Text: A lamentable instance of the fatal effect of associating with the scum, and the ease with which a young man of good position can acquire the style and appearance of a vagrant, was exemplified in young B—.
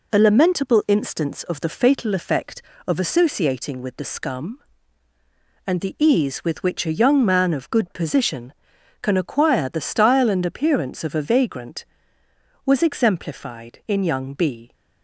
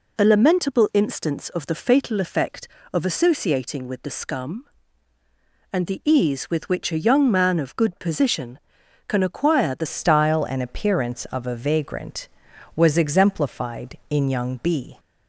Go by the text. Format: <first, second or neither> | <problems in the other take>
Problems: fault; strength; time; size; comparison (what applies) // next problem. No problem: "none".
first | changes voice at "style"; from 9.8 s on; 5.1 s long